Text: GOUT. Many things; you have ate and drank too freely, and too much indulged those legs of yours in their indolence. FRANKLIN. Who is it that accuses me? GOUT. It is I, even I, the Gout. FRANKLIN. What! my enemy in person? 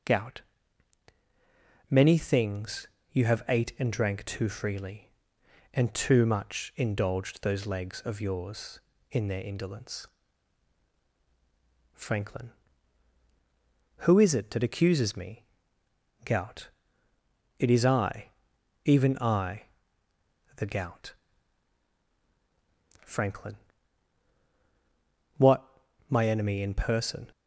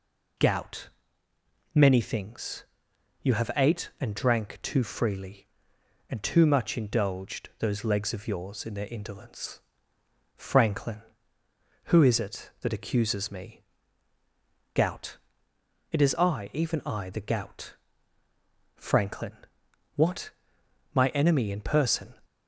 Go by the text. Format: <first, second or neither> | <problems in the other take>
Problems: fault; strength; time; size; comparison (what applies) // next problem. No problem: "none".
neither | none